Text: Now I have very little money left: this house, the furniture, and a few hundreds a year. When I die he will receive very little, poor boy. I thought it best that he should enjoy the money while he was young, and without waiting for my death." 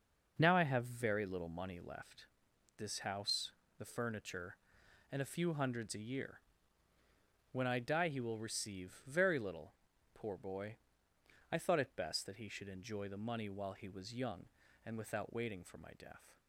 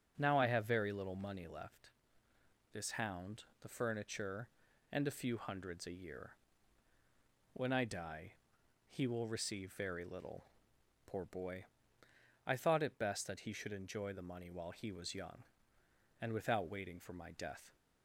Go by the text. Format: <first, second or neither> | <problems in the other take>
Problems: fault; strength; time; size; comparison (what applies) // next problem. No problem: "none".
first | starts louder than the rest; until 1.1 s; 7 dB // says "hound" for "house"; at 2.9 s // pauses between "die" and "he"; noticeable; at 8.3 s; 0.56 s long